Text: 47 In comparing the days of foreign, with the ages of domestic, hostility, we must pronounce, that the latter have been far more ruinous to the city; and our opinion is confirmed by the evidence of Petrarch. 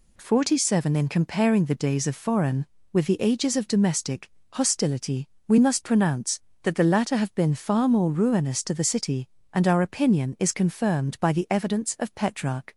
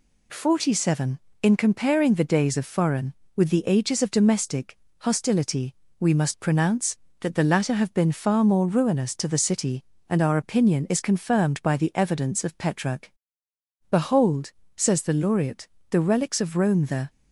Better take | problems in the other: first | goes on to say "Behold says the laureate the relics of Rome the"; strong; from 13.8 s on; 3.2 s long

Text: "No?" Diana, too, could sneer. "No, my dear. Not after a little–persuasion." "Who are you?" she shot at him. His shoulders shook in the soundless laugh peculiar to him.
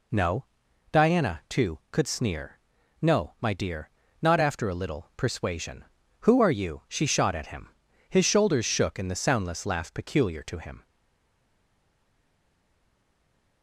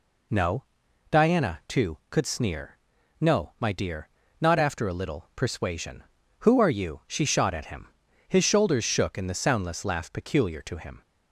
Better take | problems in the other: second | stays silent after the last word; strong; from 10.8 s on; 2.8 s long

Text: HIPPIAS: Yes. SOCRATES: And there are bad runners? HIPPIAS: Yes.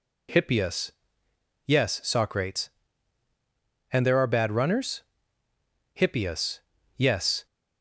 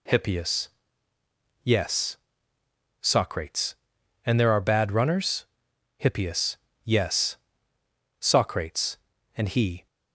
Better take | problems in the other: first | goes on to say "SOCRATES And he"; from 8.2 s on; 1.6 s long

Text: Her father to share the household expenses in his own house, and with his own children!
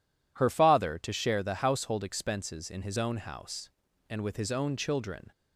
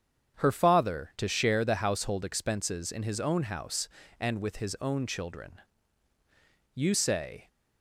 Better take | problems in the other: first | starts louder than the rest; strong; until 1.4 s; 8 dB // goes on to say "You say"; noticeable; from 6.7 s on; 0.75 s long

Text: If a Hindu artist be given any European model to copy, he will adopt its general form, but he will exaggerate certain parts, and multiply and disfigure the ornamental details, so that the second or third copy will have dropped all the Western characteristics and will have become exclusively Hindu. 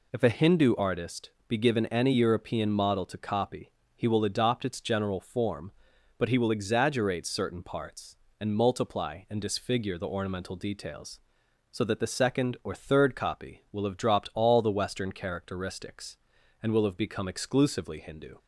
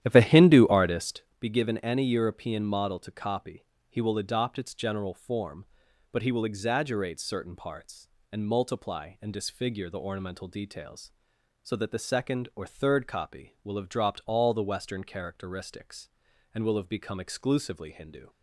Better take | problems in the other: first | starts louder than the rest; strong; until 1.4 s; 11.5 dB // pauses between "artist" and "be"; slight; at 1.2 s; 0.18 s long; slight in the first

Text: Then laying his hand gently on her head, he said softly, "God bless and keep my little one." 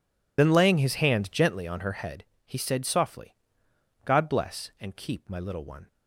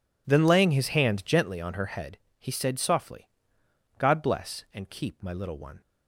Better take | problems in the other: second | loses the start of "Then"; at 0.3 s; 50 ms

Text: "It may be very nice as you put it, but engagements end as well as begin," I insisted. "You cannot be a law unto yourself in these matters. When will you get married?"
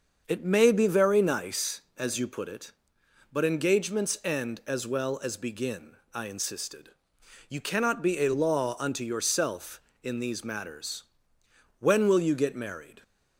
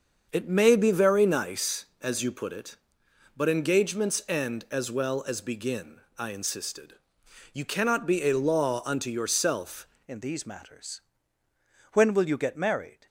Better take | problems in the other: first | starts louder than the rest; until 1.3 s; 6.5 dB; also in the first // changes voice at "in"; from 10.0 s on; 3.0 s long

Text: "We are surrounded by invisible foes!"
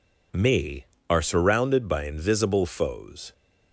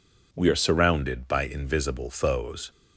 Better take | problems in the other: second | says "Me" for "We"; at 0.3 s

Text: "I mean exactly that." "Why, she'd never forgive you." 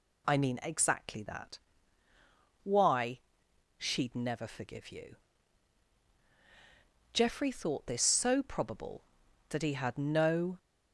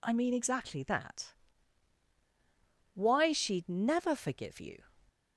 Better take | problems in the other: second | goes on to say "Geoffrey thought this so probable that he had no"; strong; from 7.1 s on; 3.4 s long

